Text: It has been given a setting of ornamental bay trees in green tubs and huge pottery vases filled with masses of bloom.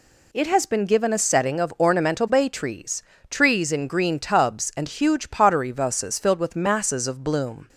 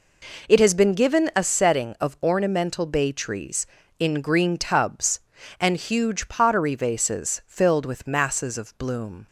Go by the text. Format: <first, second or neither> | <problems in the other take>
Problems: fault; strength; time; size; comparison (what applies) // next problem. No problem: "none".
second | says "trees" twice; at 3.2 s